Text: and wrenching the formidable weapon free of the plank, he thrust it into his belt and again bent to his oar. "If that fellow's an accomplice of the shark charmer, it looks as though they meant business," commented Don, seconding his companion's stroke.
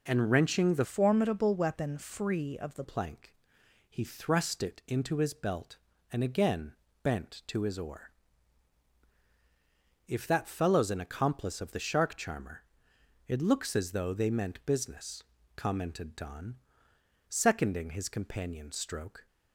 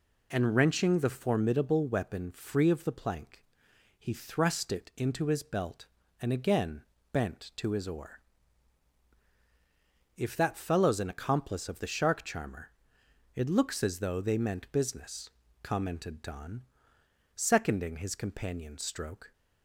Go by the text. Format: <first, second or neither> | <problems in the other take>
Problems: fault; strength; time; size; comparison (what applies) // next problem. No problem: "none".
second | changes voice from "formidable" to "the"; from 0.8 to 2.8 s; 2.0 s long // pauses between "again" and "bent"; slight; at 6.7 s; 0.30 s long; slight in the second